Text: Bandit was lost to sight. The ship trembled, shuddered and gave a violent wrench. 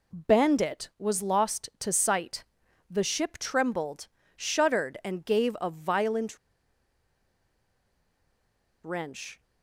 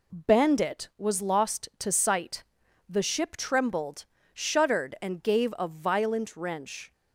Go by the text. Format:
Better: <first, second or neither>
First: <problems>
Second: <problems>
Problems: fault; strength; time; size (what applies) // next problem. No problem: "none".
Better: second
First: pauses between "violent" and "wrench"; strong; at 6.3 s; 2.4 s long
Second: none